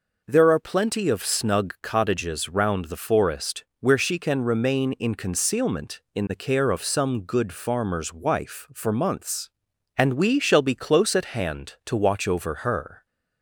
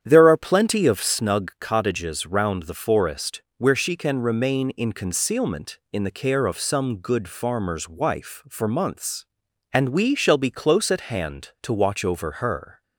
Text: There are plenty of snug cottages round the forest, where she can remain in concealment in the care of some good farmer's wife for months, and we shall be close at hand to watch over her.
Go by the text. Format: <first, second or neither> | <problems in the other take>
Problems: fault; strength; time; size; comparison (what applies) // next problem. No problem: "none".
first | starts louder than the rest; strong; until 1.2 s; 9 dB